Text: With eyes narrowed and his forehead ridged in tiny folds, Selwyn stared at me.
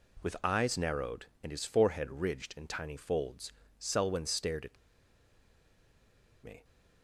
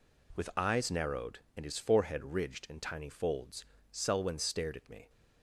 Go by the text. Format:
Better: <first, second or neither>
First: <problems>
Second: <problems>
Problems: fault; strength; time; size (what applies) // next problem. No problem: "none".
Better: second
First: pauses between "at" and "me"; strong; at 4.7 s; 1.6 s long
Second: none